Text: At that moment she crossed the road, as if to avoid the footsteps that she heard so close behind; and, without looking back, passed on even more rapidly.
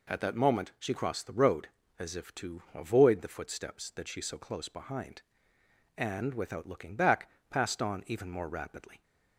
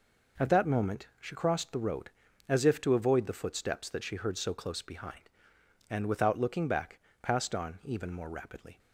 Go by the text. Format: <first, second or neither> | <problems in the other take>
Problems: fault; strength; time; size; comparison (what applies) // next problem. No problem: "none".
second | skips "heard"; at 4.2 s